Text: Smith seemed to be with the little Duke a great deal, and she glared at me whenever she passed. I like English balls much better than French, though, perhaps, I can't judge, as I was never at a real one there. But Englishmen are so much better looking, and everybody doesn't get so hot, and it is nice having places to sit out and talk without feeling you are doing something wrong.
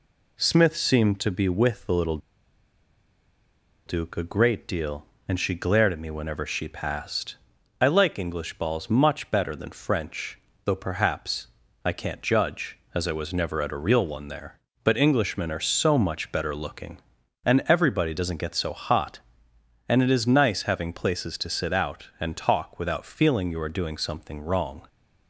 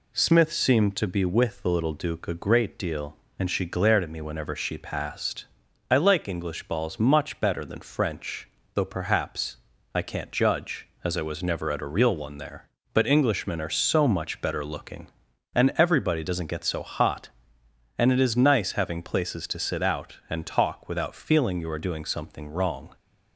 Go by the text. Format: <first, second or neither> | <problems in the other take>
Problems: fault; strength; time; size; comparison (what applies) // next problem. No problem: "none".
second | pauses between "little" and "Duke"; strong; at 2.1 s; 1.6 s long